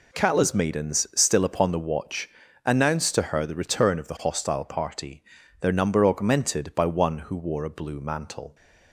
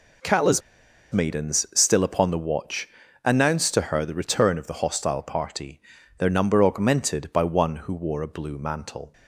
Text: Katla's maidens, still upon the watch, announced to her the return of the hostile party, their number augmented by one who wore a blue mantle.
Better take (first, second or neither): first